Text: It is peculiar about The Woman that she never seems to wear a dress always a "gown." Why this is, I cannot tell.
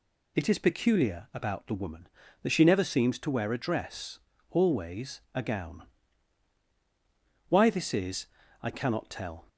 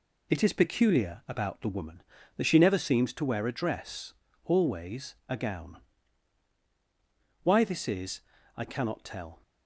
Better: first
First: pauses between "dress" and "always"; slight; at 4.1 s; 0.32 s long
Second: gets quieter; throughout; 6.5 dB // pauses between "dress" and "always"; slight; at 4.1 s; 0.32 s long

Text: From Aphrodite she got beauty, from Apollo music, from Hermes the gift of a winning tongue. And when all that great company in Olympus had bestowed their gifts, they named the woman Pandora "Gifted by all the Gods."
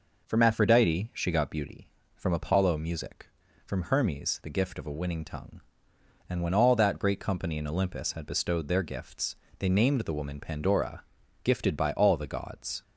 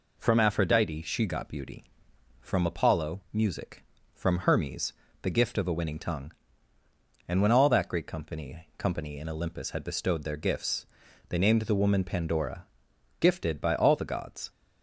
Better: first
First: pauses between "Pandora" and "Gifted"; at 11.0 s; 0.40 s long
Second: pauses between "Hermes" and "the"; slight; at 4.9 s; 0.30 s long // says "company" twice; at 8.7 s // pauses between "Pandora" and "Gifted"; noticeable; at 12.6 s; 0.54 s long

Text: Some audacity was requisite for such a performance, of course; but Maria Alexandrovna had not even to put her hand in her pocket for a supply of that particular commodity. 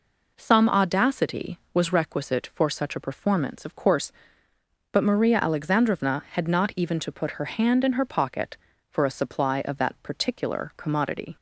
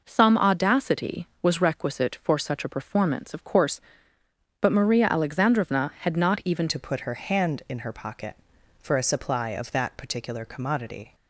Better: first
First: none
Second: changes voice at "to"; from 6.6 s on; 4.5 s long

